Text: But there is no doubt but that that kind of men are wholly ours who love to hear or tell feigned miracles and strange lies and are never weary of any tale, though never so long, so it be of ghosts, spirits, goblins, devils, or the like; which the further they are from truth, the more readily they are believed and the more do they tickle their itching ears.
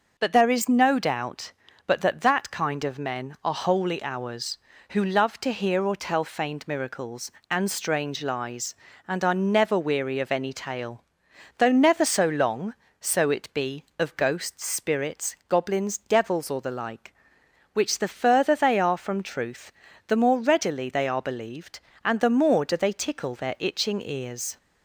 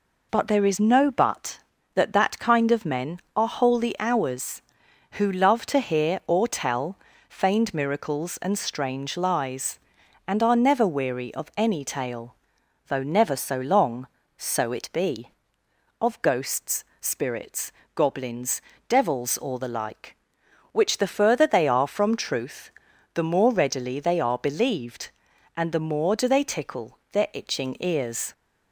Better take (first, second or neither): first